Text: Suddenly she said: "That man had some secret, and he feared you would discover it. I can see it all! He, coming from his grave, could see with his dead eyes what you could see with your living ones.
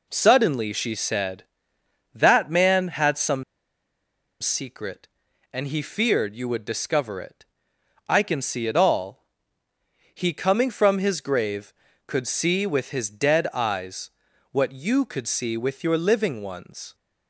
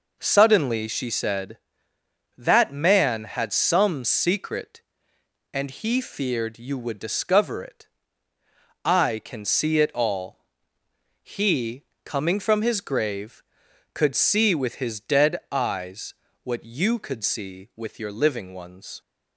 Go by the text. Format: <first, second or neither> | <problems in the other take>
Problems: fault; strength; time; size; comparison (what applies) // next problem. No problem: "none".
second | pauses between "some" and "secret"; noticeable; at 3.4 s; 0.97 s long // pauses between "eyes" and "what"; at 14.0 s; 0.42 s long; slight in the second